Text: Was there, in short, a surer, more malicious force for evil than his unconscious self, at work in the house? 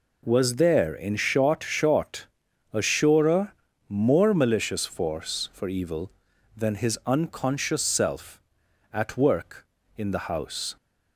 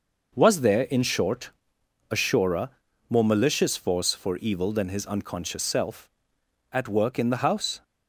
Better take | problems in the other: second | says "short" twice; at 1.6 s

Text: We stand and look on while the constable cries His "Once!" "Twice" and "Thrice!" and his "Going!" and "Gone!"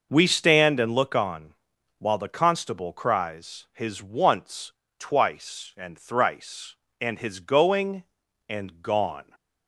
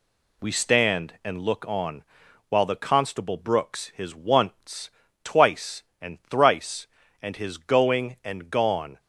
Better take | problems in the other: first | pauses between "on" and "while"; at 2.0 s; 0.44 s long; noticeable in the first // says "brooks" for "cries"; at 3.3 s

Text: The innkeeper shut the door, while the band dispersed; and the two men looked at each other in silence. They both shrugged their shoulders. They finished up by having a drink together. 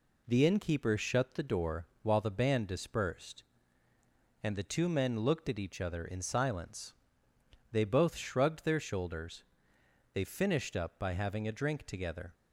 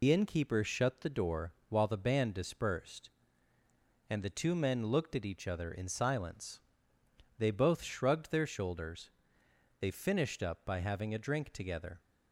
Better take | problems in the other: first | loses the start of "The"; at 0.0 s; 100 ms

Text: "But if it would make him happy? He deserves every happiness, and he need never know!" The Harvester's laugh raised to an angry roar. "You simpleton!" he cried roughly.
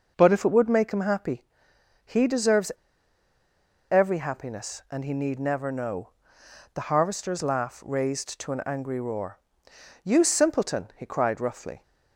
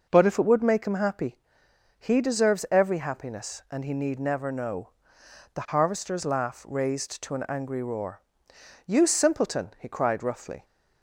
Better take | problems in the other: second | pauses between "deserves" and "every"; at 2.6 s; 1.2 s long

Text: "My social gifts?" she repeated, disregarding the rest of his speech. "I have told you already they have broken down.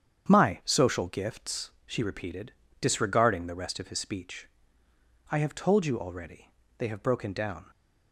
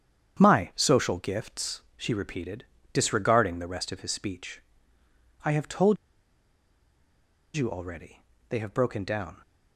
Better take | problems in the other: first | starts louder than the rest; strong; until 1.4 s; 8.5 dB; strong in the first // pauses between "told" and "you"; strong; at 5.9 s; 1.5 s long // pauses between "already" and "they"; slight; at 8.2 s; 0.28 s long; slight in the first

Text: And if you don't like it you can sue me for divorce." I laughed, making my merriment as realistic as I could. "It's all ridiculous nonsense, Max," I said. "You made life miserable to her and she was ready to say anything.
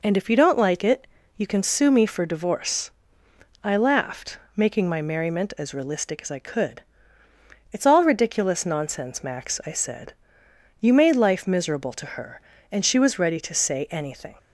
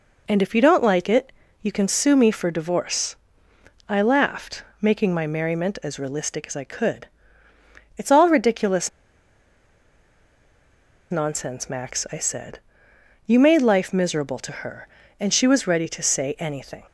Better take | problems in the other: first | pauses between "it" and "you"; slight; at 1.3 s; 0.30 s long; slight in the first // pauses between "ridiculous" and "nonsense"; strong; at 8.8 s; 2.2 s long

